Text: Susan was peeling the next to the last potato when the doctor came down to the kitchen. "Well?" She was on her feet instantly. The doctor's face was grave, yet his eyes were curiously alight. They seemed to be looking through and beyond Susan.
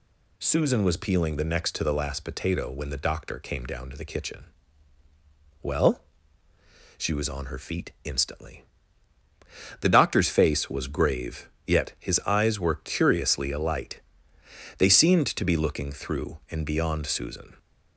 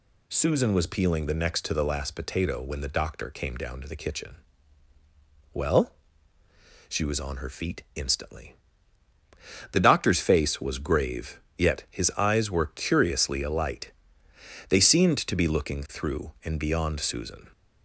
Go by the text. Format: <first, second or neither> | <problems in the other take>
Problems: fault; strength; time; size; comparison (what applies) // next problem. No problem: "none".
neither | none